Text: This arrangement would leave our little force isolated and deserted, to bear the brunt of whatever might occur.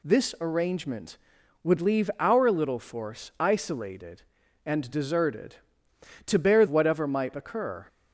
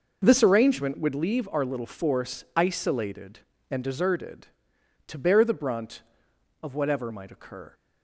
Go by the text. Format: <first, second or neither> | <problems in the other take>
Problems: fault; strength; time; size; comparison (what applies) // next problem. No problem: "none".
second | skips "the brunt of"; at 6.6 s